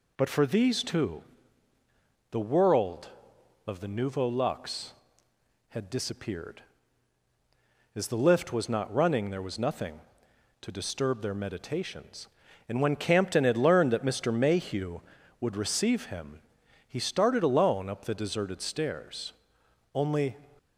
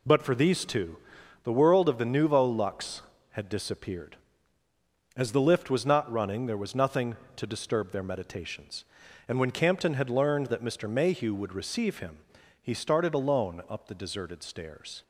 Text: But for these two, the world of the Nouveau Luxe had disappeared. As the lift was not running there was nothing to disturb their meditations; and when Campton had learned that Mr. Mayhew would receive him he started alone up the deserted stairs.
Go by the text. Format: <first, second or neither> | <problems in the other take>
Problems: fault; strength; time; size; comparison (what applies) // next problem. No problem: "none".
second | pauses between "him" and "he"; noticeable; at 16.3 s; 0.48 s long; also in the second // goes on to say "Only"; slight; from 19.9 s on; 0.44 s long